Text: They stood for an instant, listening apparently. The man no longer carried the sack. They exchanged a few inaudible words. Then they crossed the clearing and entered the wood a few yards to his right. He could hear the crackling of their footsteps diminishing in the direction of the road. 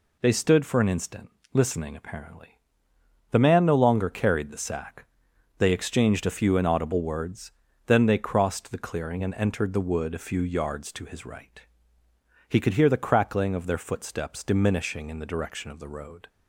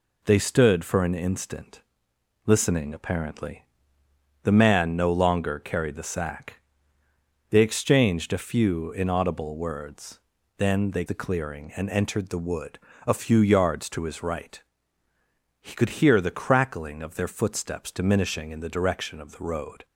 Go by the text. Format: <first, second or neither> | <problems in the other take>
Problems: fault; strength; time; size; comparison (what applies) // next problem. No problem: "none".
first | skips "crossed"; at 11.0 s // pauses between "wood" and "a"; slight; at 12.7 s; 0.30 s long